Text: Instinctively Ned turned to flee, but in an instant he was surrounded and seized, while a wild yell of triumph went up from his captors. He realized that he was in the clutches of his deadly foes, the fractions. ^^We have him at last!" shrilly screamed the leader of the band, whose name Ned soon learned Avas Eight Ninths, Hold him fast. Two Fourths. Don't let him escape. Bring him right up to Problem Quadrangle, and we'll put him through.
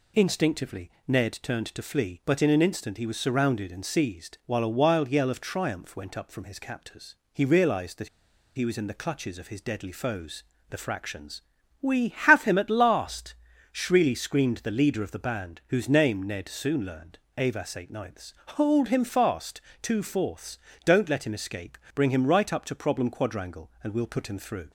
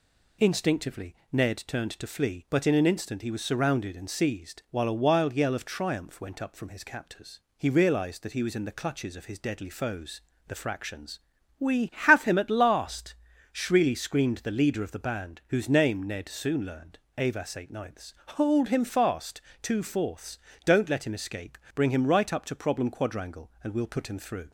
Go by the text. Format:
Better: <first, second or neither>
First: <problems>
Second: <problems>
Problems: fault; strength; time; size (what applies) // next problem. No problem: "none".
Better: second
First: pauses between "Instinctively" and "Ned"; slight; at 0.8 s; 0.18 s long // pauses between "that" and "he"; noticeable; at 8.0 s; 0.47 s long // pauses between "learned" and "Avas"; slight; at 17.1 s; 0.22 s long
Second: pauses between "Instinctively" and "Ned"; slight; at 1.1 s; 0.18 s long // pauses between "learned" and "Avas"; slight; at 16.9 s; 0.22 s long